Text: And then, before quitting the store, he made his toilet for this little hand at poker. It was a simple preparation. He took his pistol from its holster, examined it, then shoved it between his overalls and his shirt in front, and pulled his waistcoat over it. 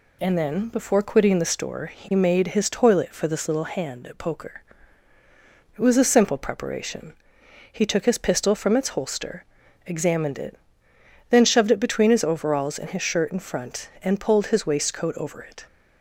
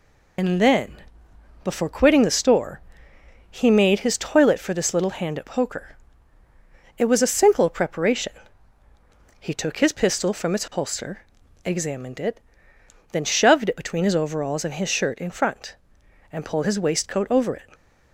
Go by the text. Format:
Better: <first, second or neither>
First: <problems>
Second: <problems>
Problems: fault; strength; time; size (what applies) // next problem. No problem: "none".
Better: first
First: none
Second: loses the start of "And"; at 0.3 s; 30 ms